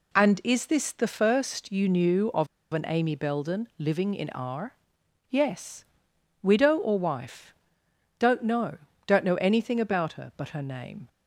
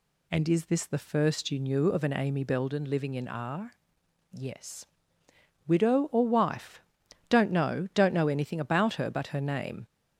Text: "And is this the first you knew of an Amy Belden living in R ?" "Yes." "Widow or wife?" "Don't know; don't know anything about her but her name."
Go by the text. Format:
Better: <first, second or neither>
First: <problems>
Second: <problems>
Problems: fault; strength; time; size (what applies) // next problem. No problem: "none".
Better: second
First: pauses between "of" and "an"; slight; at 2.4 s; 0.27 s long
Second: none